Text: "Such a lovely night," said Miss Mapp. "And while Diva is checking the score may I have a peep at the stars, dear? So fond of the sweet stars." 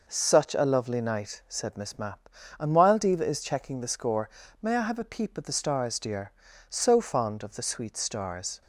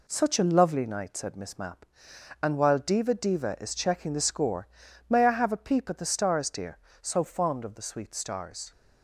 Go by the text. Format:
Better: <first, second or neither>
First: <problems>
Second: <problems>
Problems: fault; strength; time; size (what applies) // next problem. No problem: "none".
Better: first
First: pauses between "score" and "may"; slight; at 4.2 s; 0.34 s long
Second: says "Diva" twice; at 3.1 s // pauses between "score" and "may"; at 4.6 s; 0.40 s long